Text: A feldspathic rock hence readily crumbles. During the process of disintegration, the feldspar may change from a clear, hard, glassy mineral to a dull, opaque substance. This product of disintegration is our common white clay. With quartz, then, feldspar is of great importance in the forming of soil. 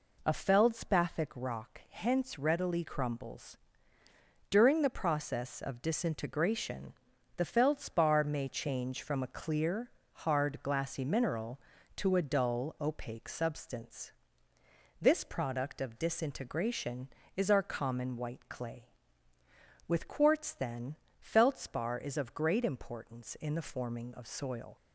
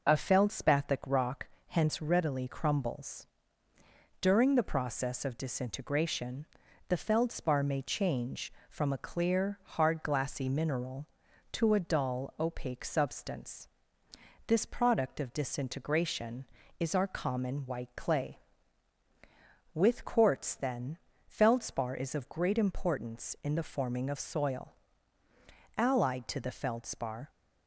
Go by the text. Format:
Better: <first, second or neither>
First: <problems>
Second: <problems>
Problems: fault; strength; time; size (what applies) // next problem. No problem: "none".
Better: first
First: none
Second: pauses between "rock" and "hence"; slight; at 1.4 s; 0.20 s long // goes on to say "Allied to the feldspar"; from 25.7 s on; 1.5 s long